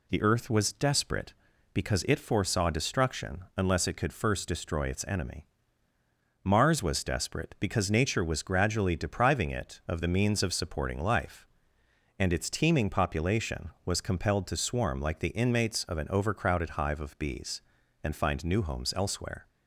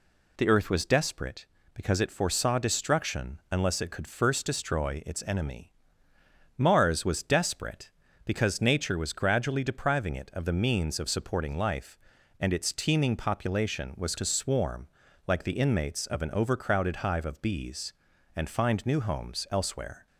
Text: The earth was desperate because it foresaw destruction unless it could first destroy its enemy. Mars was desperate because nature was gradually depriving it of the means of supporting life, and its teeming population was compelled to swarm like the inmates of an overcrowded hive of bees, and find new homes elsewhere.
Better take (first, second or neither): first